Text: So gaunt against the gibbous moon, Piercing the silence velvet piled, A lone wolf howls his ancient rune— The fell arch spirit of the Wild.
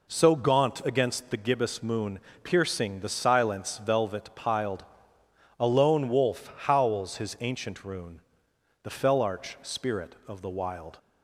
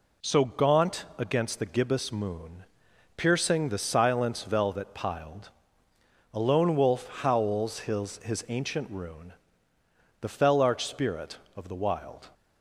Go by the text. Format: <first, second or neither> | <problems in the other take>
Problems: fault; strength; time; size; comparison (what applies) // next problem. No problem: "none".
first | says "his" twice; at 8.1 s